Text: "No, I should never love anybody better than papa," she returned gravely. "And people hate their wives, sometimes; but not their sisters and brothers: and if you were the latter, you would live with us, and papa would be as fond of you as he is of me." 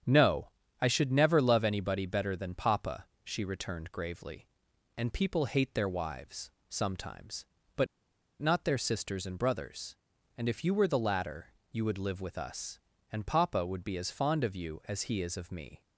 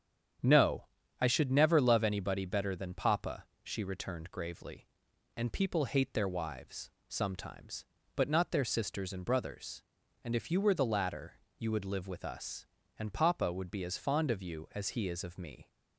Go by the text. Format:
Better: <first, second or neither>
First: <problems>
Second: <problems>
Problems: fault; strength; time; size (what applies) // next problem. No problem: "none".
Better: second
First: starts louder than the rest; strong; until 1.3 s; 8.5 dB // pauses between "but" and "not"; noticeable; at 7.8 s; 0.53 s long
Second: starts louder than the rest; strong; until 1.7 s; 8.5 dB